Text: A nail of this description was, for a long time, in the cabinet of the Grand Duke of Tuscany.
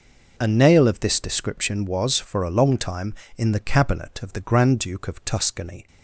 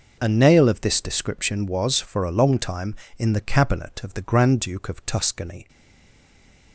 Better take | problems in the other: first | stays silent after the last word; from 5.6 s on; 1.1 s long

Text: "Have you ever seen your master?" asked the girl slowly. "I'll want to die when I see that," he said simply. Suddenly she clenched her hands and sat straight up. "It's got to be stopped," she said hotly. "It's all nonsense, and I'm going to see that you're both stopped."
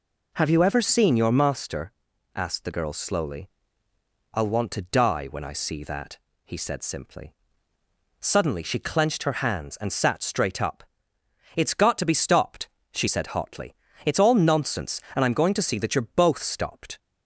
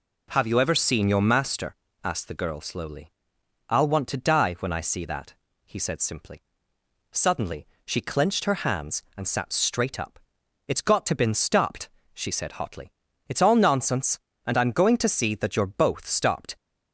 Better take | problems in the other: first | pauses between "Suddenly" and "she"; slight; at 7.6 s; 0.21 s long // says "been" for "be"; at 11.1 s

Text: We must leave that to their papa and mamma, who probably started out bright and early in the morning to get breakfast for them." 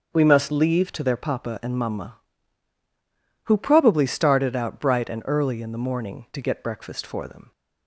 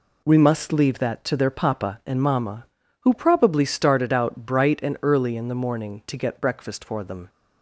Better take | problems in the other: second | starts louder than the rest; until 1.1 s; 6.5 dB // skips "that"; at 0.9 s

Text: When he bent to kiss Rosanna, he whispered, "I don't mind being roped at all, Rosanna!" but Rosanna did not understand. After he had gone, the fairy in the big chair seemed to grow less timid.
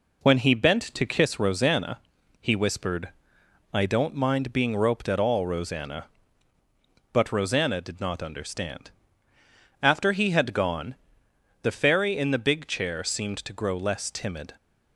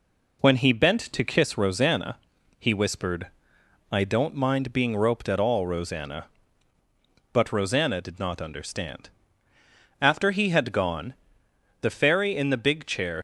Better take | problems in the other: first | stops before "seemed to grow less timid"; at 13.1 s

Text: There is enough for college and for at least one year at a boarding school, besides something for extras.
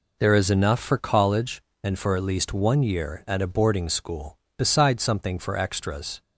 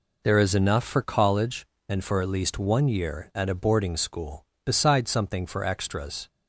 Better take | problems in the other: neither | none

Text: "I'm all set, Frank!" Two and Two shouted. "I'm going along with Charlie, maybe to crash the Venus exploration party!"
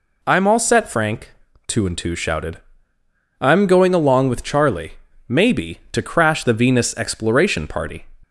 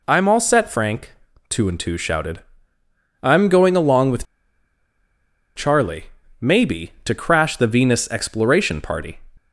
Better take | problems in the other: first | pauses between "with" and "Charlie"; strong; at 4.2 s; 1.3 s long

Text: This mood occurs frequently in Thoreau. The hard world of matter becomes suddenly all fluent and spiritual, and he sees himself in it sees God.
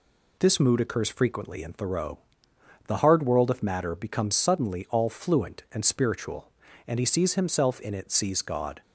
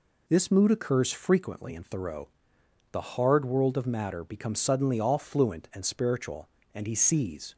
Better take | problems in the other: first | stops before "himself in it sees God"; at 7.5 s

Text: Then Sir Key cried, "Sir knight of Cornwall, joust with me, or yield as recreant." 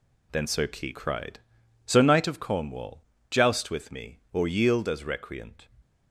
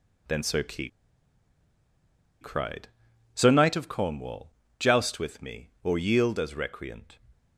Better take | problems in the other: first | pauses between "Key" and "cried"; strong; at 0.8 s; 1.5 s long

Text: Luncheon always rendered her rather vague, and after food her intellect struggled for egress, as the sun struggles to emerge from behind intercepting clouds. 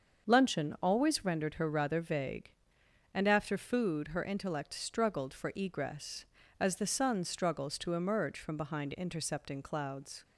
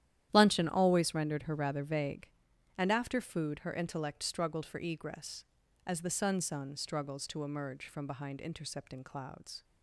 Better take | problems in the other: first | starts louder than the rest; strong; until 1.3 s; 11.5 dB; also in the first // says "sun" twice; at 6.3 s

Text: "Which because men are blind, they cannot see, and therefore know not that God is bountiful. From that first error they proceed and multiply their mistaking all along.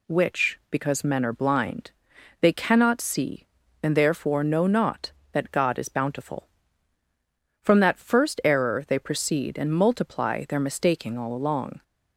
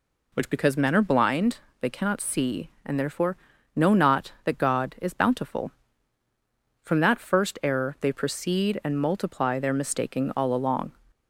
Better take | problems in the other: first | starts louder than the rest; slight; until 1.3 s; 3 dB // pauses between "therefore" and "know"; at 3.3 s; 0.38 s long

